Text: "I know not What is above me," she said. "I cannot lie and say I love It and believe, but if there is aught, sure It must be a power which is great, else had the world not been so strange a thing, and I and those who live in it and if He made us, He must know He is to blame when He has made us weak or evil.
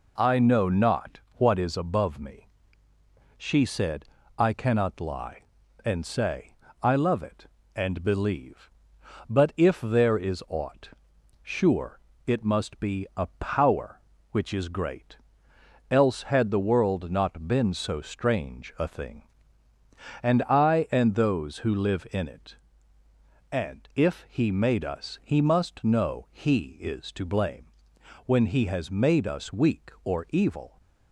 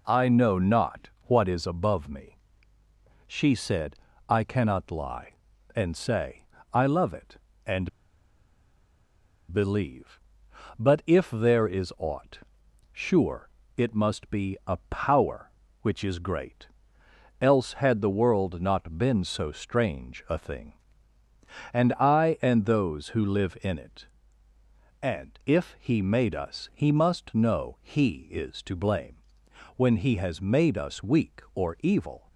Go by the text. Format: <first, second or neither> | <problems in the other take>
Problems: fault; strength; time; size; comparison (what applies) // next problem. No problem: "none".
first | pauses between "say" and "I"; slight; at 6.4 s; 0.28 s long; slight in the first // pauses between "and" and "believe"; strong; at 7.8 s; 1.6 s long // pauses between "sure" and "It"; slight; at 13.4 s; 0.28 s long; slight in the first // pauses between "blame" and "when"; noticeable; at 29.1 s; 0.60 s long; noticeable in the first